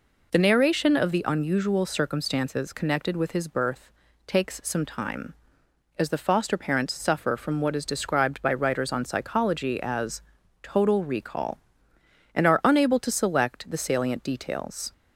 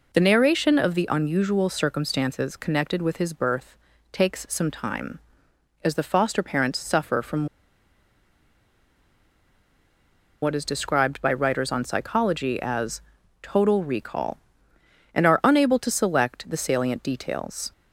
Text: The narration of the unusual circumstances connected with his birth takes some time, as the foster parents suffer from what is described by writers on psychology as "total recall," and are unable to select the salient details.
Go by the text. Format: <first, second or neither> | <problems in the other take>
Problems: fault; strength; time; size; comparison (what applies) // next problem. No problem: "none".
first | pauses between "birth" and "takes"; slight; at 3.7 s; 0.34 s long; slight in the first // pauses between "from" and "what"; strong; at 7.4 s; 2.9 s long // pauses between "as" and "total"; at 13.0 s; 0.40 s long; also in the first